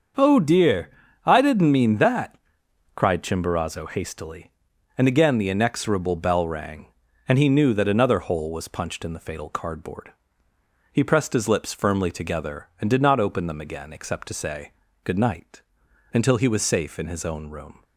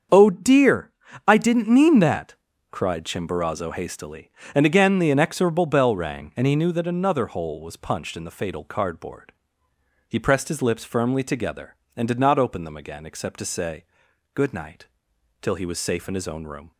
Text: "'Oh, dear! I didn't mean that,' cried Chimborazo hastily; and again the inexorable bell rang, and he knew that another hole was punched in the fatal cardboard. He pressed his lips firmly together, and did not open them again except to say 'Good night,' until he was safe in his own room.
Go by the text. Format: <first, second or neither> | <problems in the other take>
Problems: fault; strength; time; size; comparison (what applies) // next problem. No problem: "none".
first | starts louder than the rest; strong; until 1.4 s; 7 dB; also in the first // pauses between "say" and "Good"; noticeable; at 13.8 s; 0.48 s long; slight in the first // says "till" for "until"; at 15.4 s